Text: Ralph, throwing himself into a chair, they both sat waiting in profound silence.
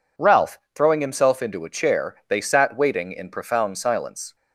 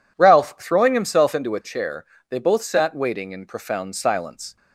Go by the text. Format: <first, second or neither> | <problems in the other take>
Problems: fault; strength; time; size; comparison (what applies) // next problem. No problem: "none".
second | skips "both"; at 2.3 s